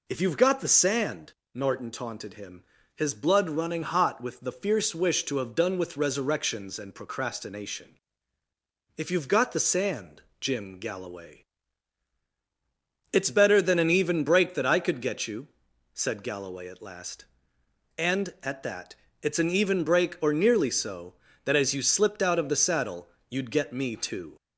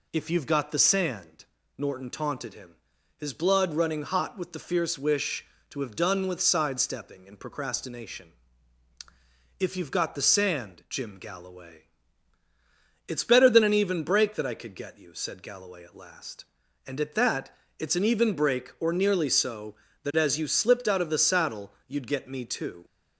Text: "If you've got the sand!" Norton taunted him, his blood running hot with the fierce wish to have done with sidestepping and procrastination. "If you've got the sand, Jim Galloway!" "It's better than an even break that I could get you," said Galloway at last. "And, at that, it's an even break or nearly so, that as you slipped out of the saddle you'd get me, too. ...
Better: second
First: says "resurrections" for "sidestepping"; at 5.9 s // pauses between "saddle" and "you'd"; slight; at 23.0 s; 0.18 s long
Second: none

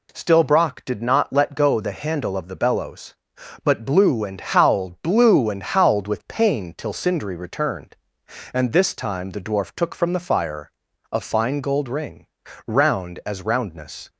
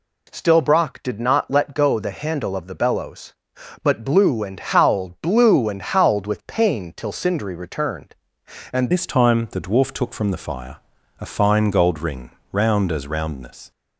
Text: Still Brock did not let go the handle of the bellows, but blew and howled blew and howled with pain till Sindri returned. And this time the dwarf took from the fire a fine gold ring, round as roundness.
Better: first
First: pauses between "fire" and "a"; at 10.7 s; 0.40 s long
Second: changes voice at "this"; from 8.9 s on; 4.8 s long // pauses between "fire" and "a"; at 10.7 s; 0.42 s long

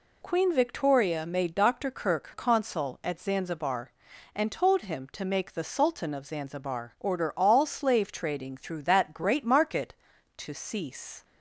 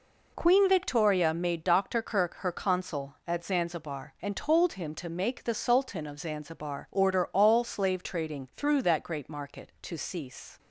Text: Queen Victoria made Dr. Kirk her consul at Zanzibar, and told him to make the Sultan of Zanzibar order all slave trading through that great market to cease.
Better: second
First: skips "her"; at 2.3 s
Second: none

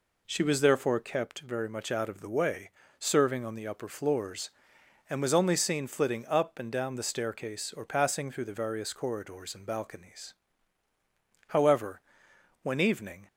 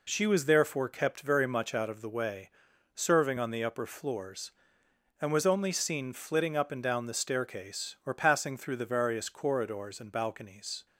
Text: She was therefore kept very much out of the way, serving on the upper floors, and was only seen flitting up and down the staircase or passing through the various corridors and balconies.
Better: second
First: goes on to say "However when evening"; strong; from 11.4 s on; 1.7 s long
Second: none

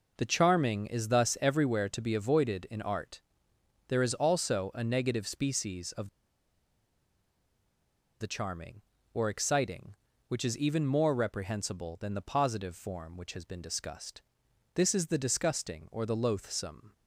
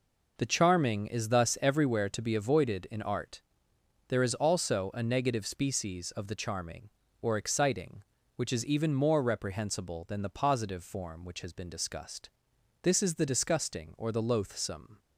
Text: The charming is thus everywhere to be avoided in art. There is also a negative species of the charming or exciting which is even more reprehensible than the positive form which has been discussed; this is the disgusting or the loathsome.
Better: second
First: pauses between "of" and "the"; strong; at 6.0 s; 2.1 s long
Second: none

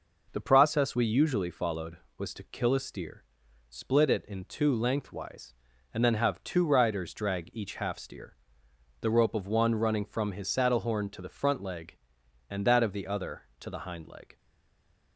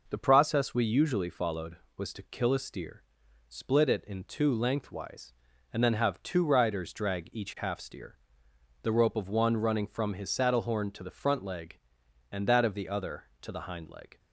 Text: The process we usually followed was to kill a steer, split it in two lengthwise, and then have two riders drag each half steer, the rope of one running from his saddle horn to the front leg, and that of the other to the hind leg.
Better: second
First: stays silent after the last word; slight; from 14.3 s on; 0.8 s long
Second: none

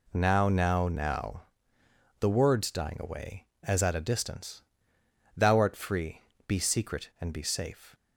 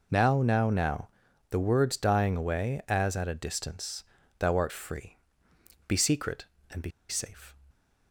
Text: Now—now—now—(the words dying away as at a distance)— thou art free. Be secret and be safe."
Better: first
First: none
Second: pauses between "be" and "safe"; slight; at 6.9 s; 0.18 s long

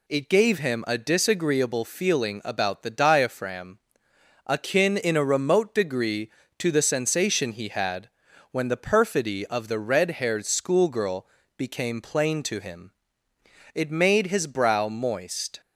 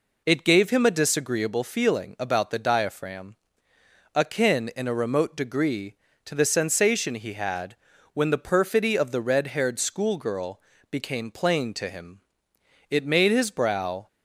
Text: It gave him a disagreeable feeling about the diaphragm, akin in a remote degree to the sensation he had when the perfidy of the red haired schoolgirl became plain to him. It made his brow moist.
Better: first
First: pauses between "had" and "when"; at 8.0 s; 0.44 s long // pauses between "schoolgirl" and "became"; slight; at 11.2 s; 0.30 s long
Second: pauses between "had" and "when"; at 7.7 s; 0.38 s long // pauses between "schoolgirl" and "became"; slight; at 10.5 s; 0.32 s long // stops before "moist"; at 14.0 s

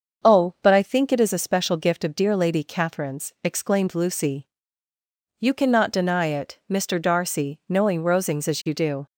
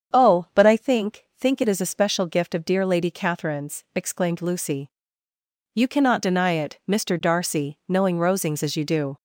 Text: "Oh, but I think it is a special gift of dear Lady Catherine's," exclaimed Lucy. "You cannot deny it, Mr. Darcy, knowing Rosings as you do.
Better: first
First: starts louder than the rest; until 1.3 s; 6.5 dB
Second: starts louder than the rest; strong; until 1.2 s; 7.5 dB // says "think" twice; at 1.3 s

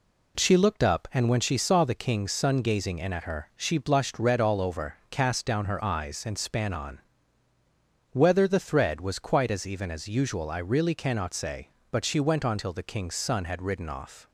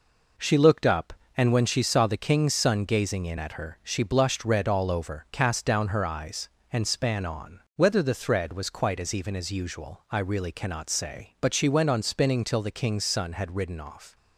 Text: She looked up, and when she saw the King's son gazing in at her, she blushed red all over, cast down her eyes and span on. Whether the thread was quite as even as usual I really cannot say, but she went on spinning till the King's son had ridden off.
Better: second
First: skips "spinning"; at 12.5 s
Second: none

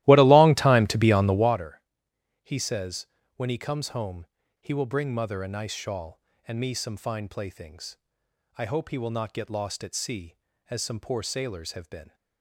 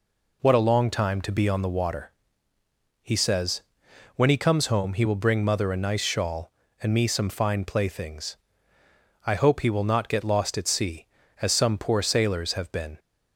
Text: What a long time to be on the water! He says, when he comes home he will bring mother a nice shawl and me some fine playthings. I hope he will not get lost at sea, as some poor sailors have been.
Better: second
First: starts louder than the rest; strong; until 1.6 s; 16 dB // pauses between "home" and "he"; slight; at 4.2 s; 0.35 s long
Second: none

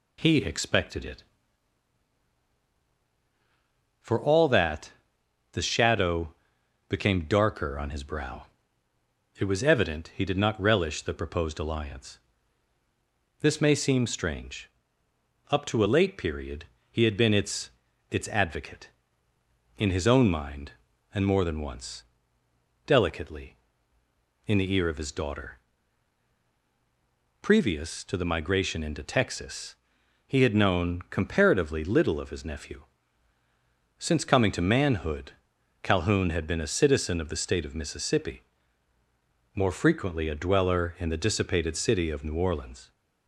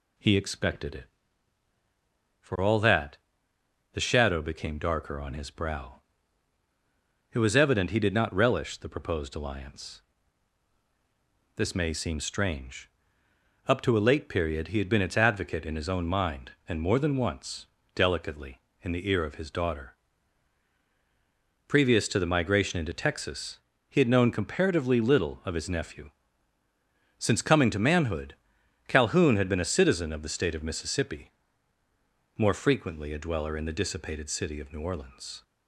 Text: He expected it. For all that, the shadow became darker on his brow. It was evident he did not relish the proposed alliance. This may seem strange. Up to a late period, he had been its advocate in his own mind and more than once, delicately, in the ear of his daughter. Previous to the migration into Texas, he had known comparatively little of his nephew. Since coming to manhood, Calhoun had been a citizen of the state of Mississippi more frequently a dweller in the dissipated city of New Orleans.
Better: second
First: pauses between "shadow" and "became"; noticeable; at 6.3 s; 0.56 s long // says "its" twice; at 18.0 s // pauses between "Mississippi" and "more"; at 38.4 s; 1.1 s long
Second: pauses between "Mississippi" and "more"; at 31.3 s; 1.1 s long

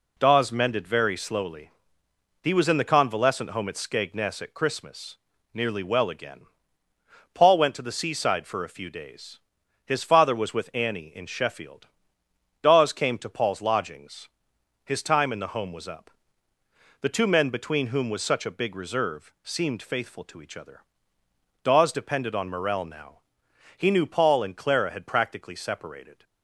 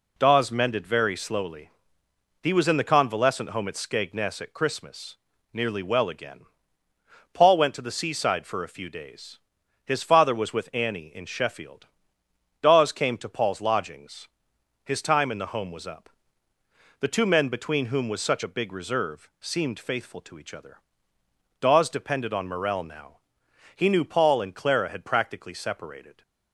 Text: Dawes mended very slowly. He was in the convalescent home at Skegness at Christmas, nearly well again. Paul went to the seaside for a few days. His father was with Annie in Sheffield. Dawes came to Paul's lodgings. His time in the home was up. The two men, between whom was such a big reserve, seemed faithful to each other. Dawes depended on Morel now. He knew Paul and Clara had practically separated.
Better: neither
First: none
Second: none

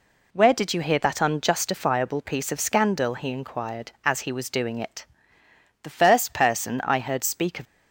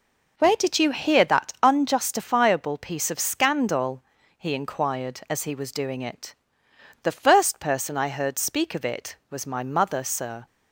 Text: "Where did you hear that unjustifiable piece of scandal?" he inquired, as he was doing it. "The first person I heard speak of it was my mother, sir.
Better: second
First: stops before "it was my mother sir"; at 7.6 s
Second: none

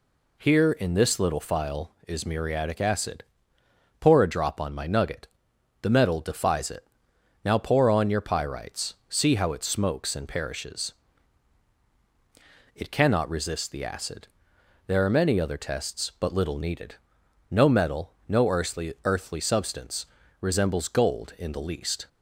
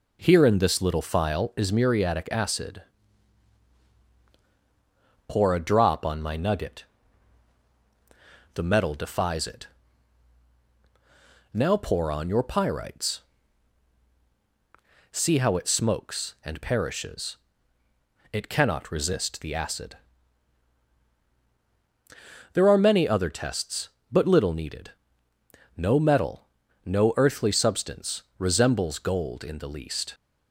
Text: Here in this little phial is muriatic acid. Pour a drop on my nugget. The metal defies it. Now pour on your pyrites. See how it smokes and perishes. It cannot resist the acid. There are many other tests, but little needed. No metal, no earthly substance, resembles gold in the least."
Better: second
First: says "earthly" twice; at 19.0 s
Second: none

